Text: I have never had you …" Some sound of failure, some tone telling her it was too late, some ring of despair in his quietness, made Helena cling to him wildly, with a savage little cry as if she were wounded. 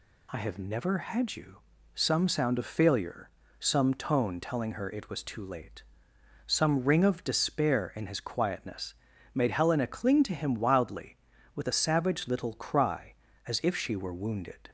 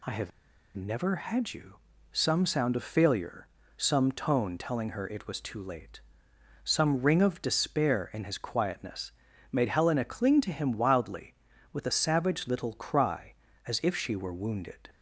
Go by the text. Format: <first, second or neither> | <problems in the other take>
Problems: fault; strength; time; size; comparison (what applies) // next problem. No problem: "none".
first | pauses between "have" and "never"; noticeable; at 0.3 s; 0.46 s long